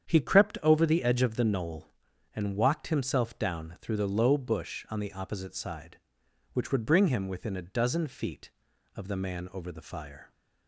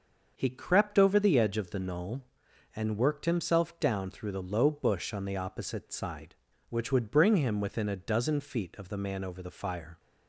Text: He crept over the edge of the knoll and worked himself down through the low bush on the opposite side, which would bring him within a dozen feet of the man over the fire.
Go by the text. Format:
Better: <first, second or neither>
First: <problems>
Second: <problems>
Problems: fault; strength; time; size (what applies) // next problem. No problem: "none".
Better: second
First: starts louder than the rest; strong; until 1.1 s; 8.5 dB // says "walked" for "worked"; at 2.5 s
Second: starts louder than the rest; until 1.3 s; 6.5 dB